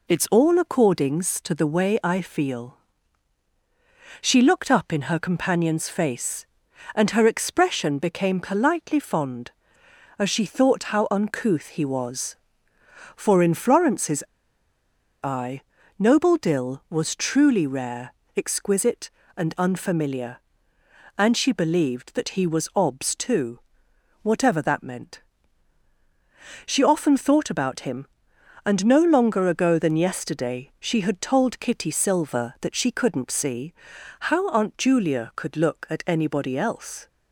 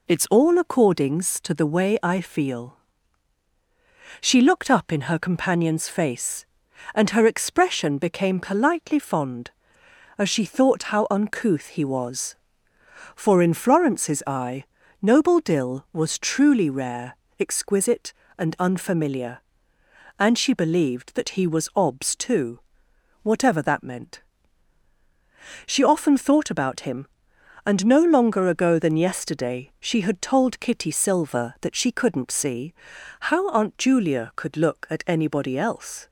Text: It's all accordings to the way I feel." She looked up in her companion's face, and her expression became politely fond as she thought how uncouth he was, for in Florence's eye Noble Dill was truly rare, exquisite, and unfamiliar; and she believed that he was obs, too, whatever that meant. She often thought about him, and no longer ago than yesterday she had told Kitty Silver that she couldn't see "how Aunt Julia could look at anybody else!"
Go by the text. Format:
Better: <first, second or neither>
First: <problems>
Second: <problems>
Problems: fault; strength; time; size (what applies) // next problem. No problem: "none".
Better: second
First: pauses between "Florence's" and "eye"; at 14.2 s; 1.0 s long // pauses between "eye" and "Noble"; at 15.5 s; 0.40 s long // pauses between "see" and "how"; noticeable; at 33.7 s; 0.58 s long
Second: pauses between "eye" and "Noble"; at 14.6 s; 0.40 s long // pauses between "see" and "how"; noticeable; at 32.7 s; 0.58 s long